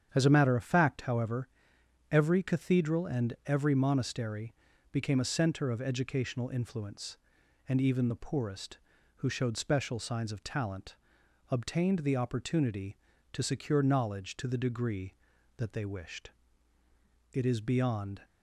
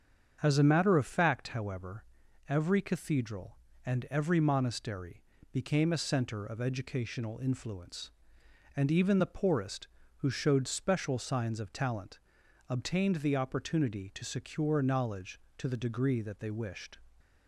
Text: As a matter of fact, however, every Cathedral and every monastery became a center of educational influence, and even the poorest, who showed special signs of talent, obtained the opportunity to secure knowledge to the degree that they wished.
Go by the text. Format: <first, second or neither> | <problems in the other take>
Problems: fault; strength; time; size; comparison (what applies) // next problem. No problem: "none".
second | starts louder than the rest; strong; until 1.1 s; 8.5 dB; strong in the second // pauses between "monastery" and "became"; at 4.5 s; 0.38 s long; slight in the second // goes on to say "It is beyond"; noticeable; from 17.3 s on; 0.90 s long